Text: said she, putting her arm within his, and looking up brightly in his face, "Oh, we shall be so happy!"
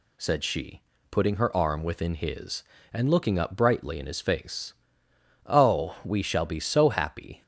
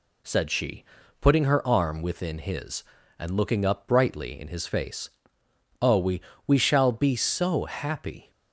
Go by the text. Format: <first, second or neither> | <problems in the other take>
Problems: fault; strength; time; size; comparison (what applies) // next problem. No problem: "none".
first | says "we" twice; at 6.4 s